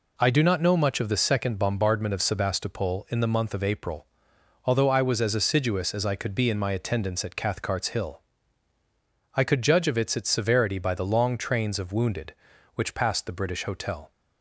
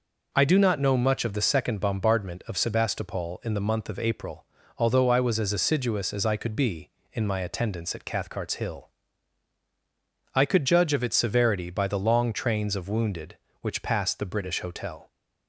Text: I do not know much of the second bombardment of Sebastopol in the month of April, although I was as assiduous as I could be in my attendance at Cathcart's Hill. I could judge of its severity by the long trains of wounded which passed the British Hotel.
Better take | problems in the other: second | says "its" twice; at 10.1 s

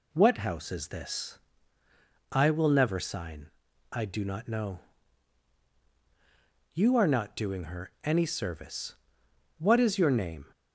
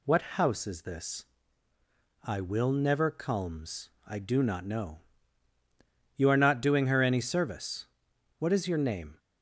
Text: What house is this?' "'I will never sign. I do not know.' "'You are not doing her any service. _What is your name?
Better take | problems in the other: first | says "culms" for "sign"; at 3.1 s

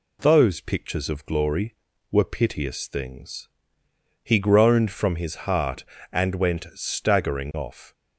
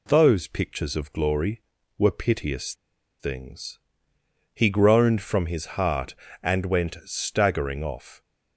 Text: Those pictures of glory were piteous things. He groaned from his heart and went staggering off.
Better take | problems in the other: first | pauses between "piteous" and "things"; noticeable; at 2.7 s; 0.46 s long

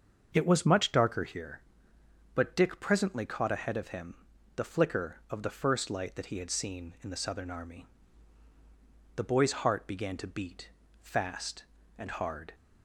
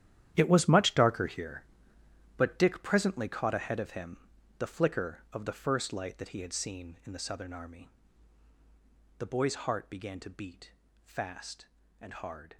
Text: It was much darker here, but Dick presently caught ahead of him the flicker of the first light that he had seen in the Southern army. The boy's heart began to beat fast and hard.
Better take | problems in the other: first | gets quieter; strong; throughout; 14 dB // starts louder than the rest; strong; until 1.3 s; 10.5 dB; also in the first // pauses between "him" and "the"; at 4.1 s; 0.42 s long; also in the first // pauses between "beat" and "fast"; slight; at 10.7 s; 0.32 s long; slight in the first

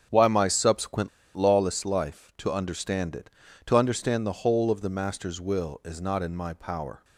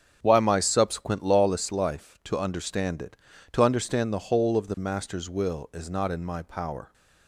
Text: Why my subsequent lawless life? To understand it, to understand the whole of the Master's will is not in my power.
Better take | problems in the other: second | starts louder than the rest; strong; until 1.3 s; 8.5 dB; strong in the second // pauses between "subsequent" and "lawless"; slight; at 1.0 s; 0.27 s long

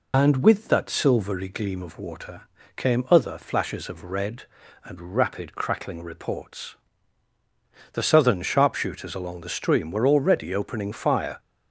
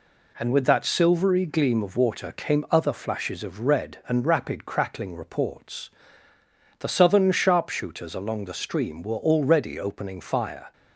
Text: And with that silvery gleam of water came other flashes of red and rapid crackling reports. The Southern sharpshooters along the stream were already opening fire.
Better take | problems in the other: second | loses the start of "And"; at 0.1 s; 60 ms // pauses between "water" and "came"; slight; at 2.4 s; 0.34 s long

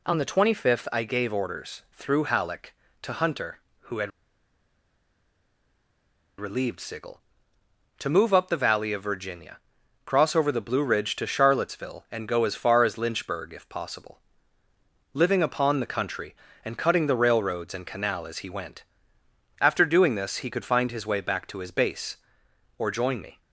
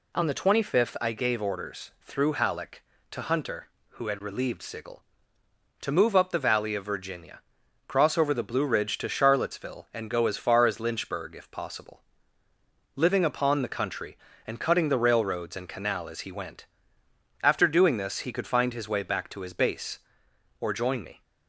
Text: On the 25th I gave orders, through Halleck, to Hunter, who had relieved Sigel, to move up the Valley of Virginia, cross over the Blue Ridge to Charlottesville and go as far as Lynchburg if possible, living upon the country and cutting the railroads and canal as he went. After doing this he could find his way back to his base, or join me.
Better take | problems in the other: second | pauses between "had" and "relieved"; strong; at 4.1 s; 2.2 s long

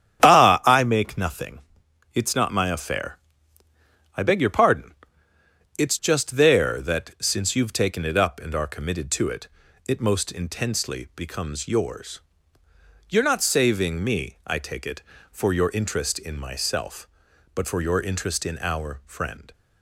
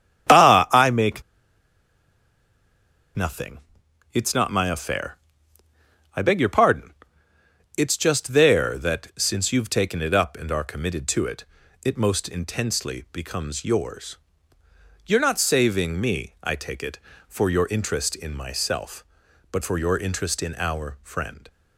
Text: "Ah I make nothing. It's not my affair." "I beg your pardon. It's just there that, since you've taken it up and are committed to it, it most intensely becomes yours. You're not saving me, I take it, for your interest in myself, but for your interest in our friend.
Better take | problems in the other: first | starts louder than the rest; strong; until 3.2 s; 10 dB; strong in the first // pauses between "make" and "nothing"; strong; at 1.2 s; 1.9 s long

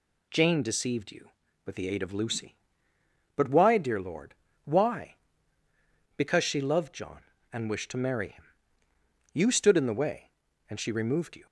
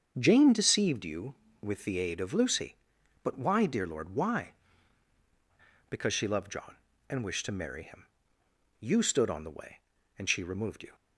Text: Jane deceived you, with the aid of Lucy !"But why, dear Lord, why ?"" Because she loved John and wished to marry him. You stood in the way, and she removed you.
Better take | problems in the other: first | starts louder than the rest; strong; until 1.1 s; 7.5 dB // says "on" for "in"; at 9.2 s

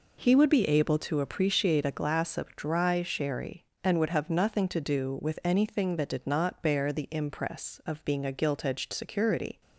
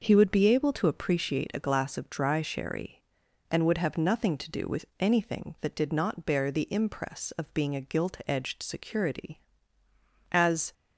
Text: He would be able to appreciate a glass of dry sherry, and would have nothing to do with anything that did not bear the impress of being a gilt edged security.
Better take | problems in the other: first | goes on to say "As"; slight; from 10.3 s on; 0.42 s long

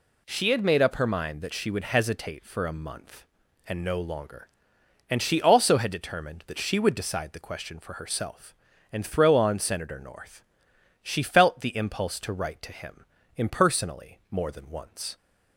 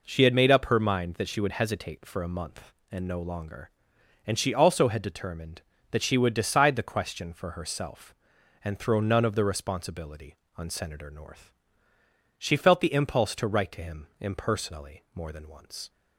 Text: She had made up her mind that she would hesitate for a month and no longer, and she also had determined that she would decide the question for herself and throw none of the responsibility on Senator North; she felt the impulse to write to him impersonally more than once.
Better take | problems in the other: second | skips "none of the responsibility"; at 9.3 s // pauses between "him" and "impersonally"; slight; at 13.0 s; 0.32 s long

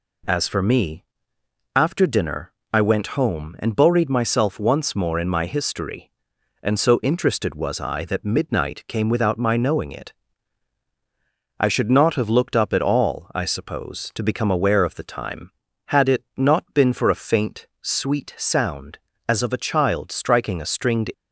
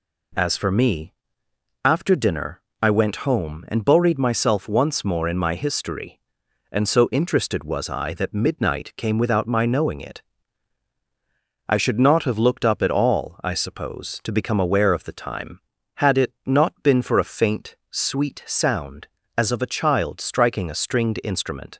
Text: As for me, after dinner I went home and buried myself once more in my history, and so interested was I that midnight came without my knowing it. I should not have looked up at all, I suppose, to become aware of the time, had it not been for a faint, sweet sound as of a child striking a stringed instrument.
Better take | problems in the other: second | pauses between "dinner" and "I"; slight; at 2.5 s; 0.22 s long; slight in the second // stops before "instrument"; at 21.1 s

